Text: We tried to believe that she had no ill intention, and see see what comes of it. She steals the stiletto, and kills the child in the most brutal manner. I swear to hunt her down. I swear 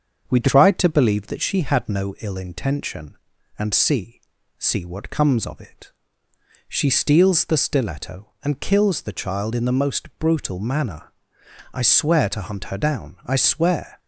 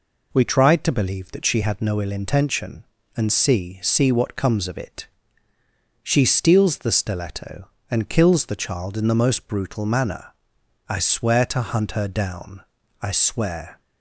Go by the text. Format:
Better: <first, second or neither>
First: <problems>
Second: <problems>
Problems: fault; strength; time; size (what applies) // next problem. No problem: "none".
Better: second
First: starts louder than the rest; until 1.5 s; 6.5 dB // pauses between "see" and "see"; at 4.2 s; 0.38 s long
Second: none